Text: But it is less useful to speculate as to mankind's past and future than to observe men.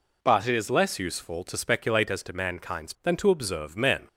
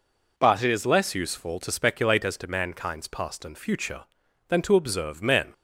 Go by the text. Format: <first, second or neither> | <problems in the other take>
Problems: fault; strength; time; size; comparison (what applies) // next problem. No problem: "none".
second | skips "past and future"; at 2.9 s